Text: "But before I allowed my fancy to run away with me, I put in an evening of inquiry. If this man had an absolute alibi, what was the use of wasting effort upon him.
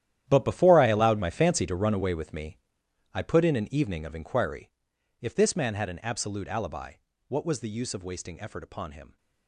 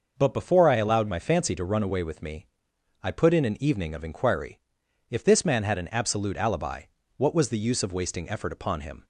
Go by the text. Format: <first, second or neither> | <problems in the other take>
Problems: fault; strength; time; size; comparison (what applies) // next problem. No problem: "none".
second | gets quieter; strong; throughout; 14.5 dB // starts louder than the rest; strong; until 1.2 s; 11.5 dB; noticeable in the second